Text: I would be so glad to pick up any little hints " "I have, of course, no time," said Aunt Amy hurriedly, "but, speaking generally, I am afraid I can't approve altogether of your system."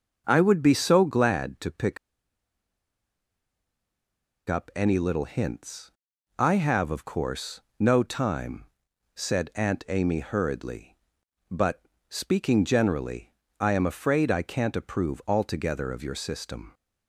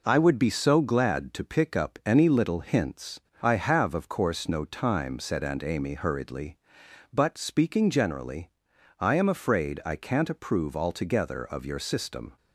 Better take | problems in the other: second | starts louder than the rest; until 1.2 s; 6.5 dB // pauses between "pick" and "up"; strong; at 1.9 s; 2.5 s long

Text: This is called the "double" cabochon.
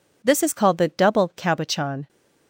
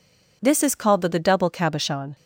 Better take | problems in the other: first | says "the" twice; at 1.0 s

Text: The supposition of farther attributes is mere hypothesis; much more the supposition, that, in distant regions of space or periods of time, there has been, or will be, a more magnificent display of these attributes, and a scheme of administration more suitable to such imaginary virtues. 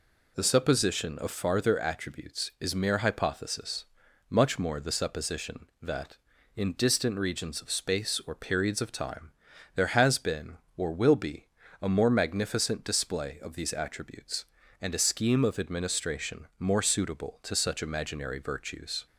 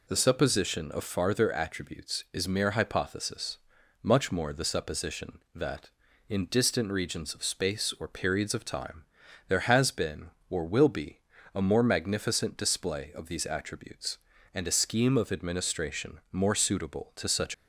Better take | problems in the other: first | stops before "imaginary virtues"; at 17.5 s

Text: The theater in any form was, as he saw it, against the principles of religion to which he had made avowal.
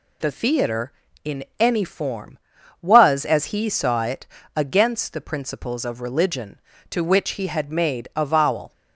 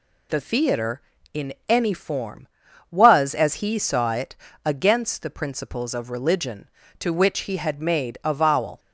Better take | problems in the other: neither | pauses between "in" and "any"; slight; the same in both

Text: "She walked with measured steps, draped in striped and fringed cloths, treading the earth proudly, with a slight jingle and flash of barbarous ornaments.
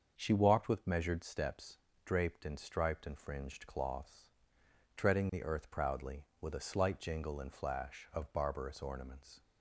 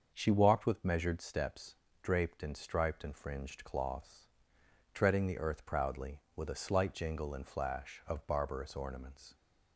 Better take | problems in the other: neither | starts louder than the rest; the same in both

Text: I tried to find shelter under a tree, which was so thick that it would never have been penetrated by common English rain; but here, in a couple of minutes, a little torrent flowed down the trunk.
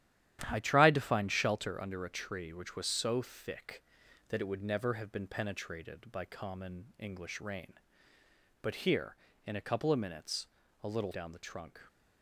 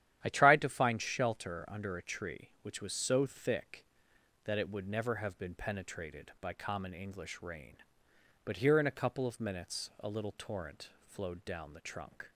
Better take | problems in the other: second | starts louder than the rest; strong; until 1.4 s; 11.5 dB; strong in the second // skips "torrent flowed"; at 11.1 s

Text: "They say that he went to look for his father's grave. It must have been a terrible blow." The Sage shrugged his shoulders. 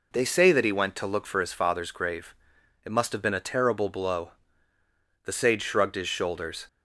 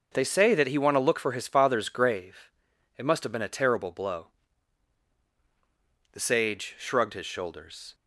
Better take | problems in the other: first | says "want" for "went"; at 0.7 s

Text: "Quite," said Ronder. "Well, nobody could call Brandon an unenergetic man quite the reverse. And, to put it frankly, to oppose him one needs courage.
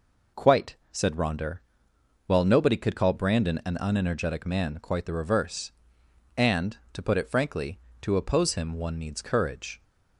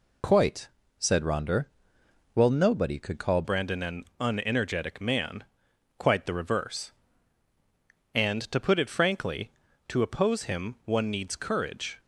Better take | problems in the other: first | changes voice at "Brandon"; from 3.4 s on; 8.5 s long // pauses between "man" and "quite"; noticeable; at 5.4 s; 0.56 s long

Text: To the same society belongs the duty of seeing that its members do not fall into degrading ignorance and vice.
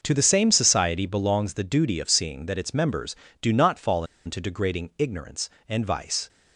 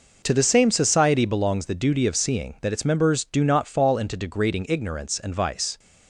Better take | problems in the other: second | starts louder than the rest; noticeable; until 1.0 s; 6 dB // pauses between "fall" and "into"; slight; at 4.0 s; 0.20 s long

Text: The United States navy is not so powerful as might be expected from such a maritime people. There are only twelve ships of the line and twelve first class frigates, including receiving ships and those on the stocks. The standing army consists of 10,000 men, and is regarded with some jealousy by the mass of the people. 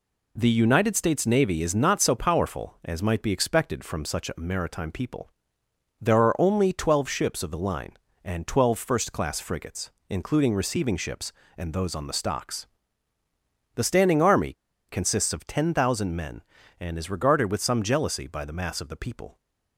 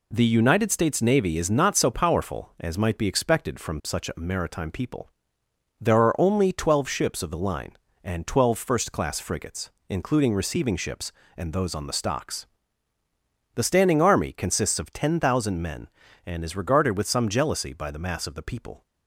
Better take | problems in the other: second | pauses between "army" and "consists"; slight; at 14.5 s; 0.36 s long

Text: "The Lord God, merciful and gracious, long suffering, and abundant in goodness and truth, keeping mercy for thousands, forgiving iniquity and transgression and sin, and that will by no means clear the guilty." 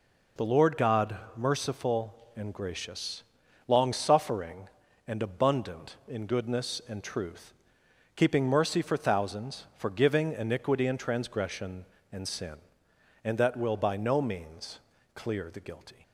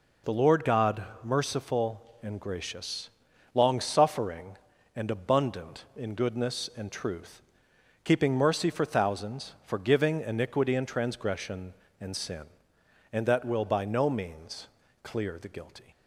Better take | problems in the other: neither | pauses between "means" and "clear"; slight; the same in both

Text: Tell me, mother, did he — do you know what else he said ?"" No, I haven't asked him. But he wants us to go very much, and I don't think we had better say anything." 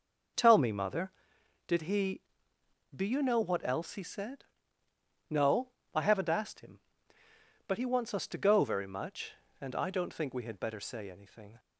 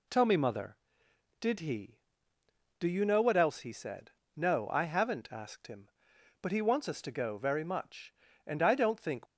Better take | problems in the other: first | stops before "we had better say anything"; at 9.2 s

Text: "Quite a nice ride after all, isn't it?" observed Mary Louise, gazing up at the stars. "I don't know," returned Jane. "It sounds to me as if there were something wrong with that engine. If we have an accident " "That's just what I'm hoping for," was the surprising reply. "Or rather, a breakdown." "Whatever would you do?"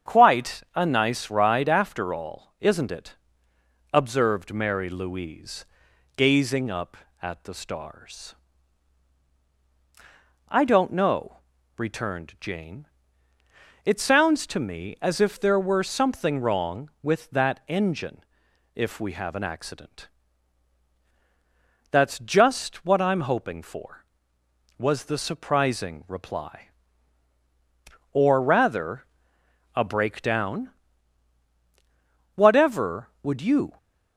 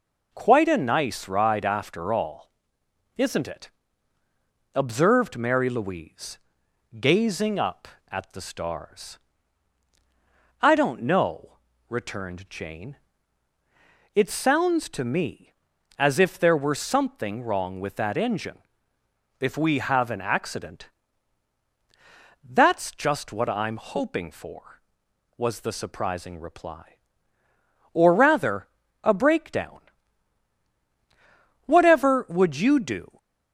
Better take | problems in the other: second | starts louder than the rest; strong; until 1.1 s; 8 dB // stops before "do"; at 33.7 s

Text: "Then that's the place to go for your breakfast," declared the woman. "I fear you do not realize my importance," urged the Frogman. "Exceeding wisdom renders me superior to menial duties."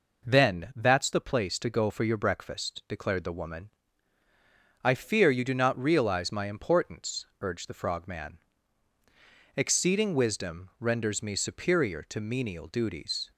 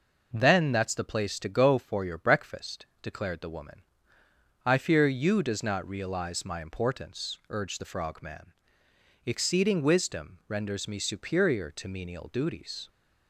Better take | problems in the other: first | says "does" for "do"; at 5.4 s

